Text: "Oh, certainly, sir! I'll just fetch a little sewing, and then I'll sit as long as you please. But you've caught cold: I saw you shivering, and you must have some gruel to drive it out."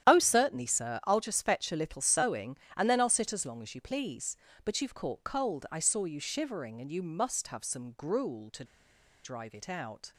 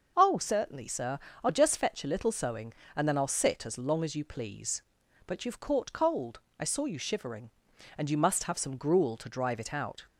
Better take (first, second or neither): second